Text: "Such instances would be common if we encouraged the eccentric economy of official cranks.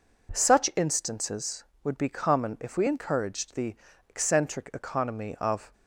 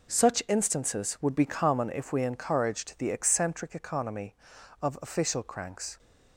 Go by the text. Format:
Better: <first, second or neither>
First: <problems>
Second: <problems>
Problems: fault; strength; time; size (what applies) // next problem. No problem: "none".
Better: second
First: pauses between "the" and "eccentric"; slight; at 3.7 s; 0.36 s long // stops before "official cranks"; at 5.7 s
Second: none